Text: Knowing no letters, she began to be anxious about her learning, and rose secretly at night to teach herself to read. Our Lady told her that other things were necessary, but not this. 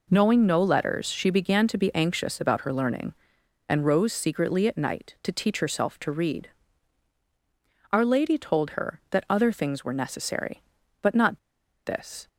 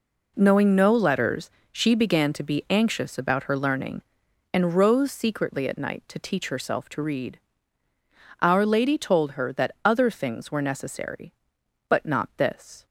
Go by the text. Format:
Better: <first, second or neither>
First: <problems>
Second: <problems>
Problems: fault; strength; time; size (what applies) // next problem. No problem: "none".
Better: second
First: pauses between "not" and "this"; noticeable; at 11.3 s; 0.47 s long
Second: none